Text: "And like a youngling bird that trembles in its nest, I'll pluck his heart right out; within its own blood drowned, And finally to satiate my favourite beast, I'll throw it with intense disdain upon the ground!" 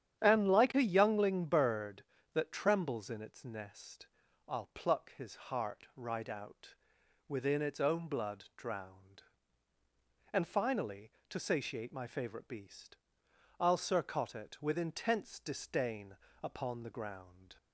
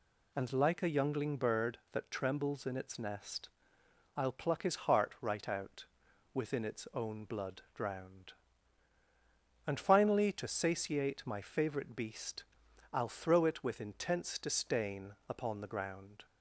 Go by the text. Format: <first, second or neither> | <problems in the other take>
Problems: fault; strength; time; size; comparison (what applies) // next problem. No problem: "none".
second | starts louder than the rest; strong; until 1.2 s; 9.5 dB // says "surcot" for "throw"; at 13.7 s // pauses between "disdain" and "upon"; slight; at 16.1 s; 0.26 s long